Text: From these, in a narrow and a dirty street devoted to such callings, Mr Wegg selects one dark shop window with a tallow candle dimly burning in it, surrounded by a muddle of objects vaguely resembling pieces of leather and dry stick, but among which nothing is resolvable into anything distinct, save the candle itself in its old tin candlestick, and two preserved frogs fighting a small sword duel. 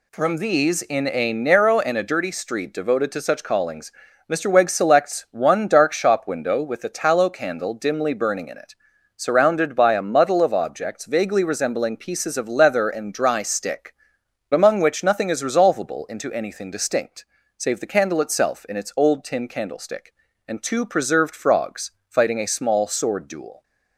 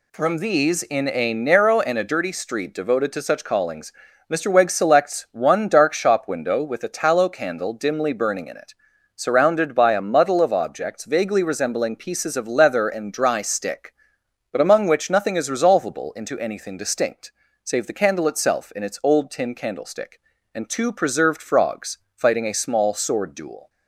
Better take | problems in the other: second | skips "but"; at 14.2 s // pauses between "frogs" and "fighting"; slight; at 21.9 s; 0.16 s long; slight in the second

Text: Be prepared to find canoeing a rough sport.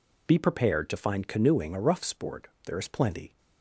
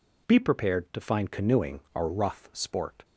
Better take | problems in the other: second | goes on to say "There is plenty"; noticeable; from 2.6 s on; 0.72 s long

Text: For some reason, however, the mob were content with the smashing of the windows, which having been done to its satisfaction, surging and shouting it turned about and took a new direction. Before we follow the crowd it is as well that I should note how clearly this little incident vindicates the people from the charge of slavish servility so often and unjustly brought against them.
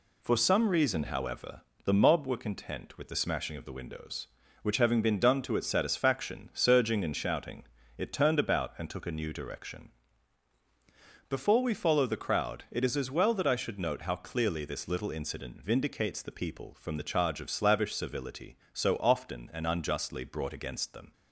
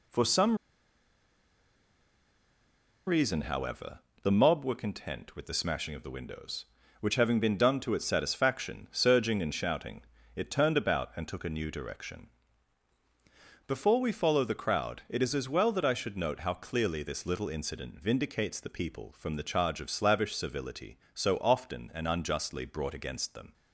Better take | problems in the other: first | pauses between "some" and "reason"; strong; at 0.5 s; 2.5 s long // pauses between "shouting" and "it"; slight; at 10.0 s; 0.32 s long; slight in the first

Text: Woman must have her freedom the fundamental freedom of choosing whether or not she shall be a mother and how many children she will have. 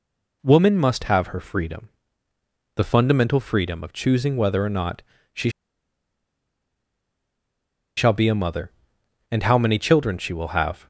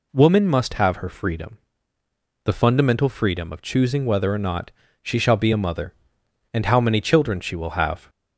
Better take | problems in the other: second | pauses between "freedom" and "the"; noticeable; at 1.8 s; 0.86 s long; noticeable in the second // pauses between "not" and "she"; slight; at 5.0 s; 0.32 s long; slight in the second // pauses between "she" and "shall"; strong; at 5.4 s; 2.4 s long

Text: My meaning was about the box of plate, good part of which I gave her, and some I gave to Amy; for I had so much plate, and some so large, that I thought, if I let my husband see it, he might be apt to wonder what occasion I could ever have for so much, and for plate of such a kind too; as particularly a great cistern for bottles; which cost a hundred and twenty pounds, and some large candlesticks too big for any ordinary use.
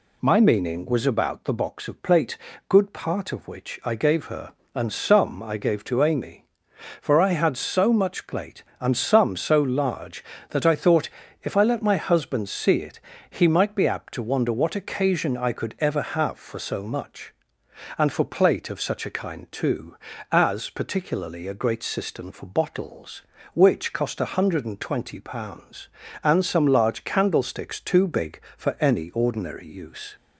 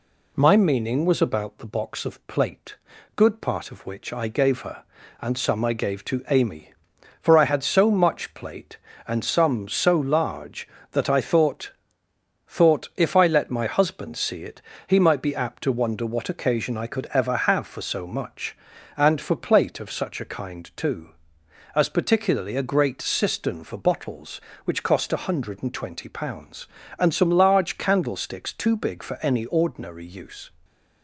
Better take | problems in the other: first | says "thought" twice; at 12.4 s

